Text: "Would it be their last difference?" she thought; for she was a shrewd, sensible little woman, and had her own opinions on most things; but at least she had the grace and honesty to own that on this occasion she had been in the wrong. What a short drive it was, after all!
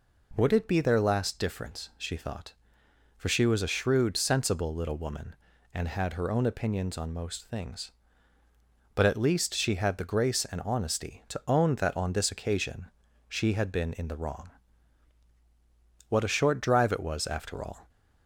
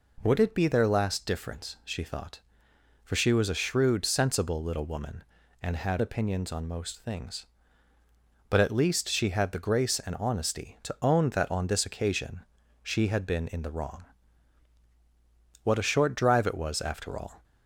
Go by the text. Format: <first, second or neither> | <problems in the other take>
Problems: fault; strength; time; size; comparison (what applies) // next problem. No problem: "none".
first | skips "her own"; at 6.0 s // pauses between "occasion" and "she"; at 12.4 s; 0.38 s long; also in the first